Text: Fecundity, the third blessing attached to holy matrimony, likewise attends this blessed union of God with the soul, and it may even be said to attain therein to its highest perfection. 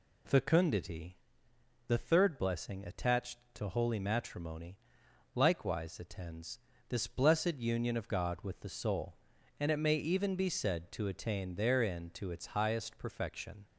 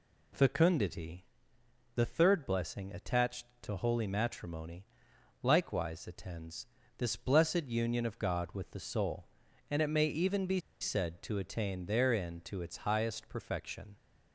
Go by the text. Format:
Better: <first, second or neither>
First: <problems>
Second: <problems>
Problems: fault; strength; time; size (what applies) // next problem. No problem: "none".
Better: first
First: pauses between "attends" and "this"; slight; at 6.5 s; 0.31 s long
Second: pauses between "attends" and "this"; slight; at 6.6 s; 0.32 s long // pauses between "be" and "said"; slight; at 10.5 s; 0.23 s long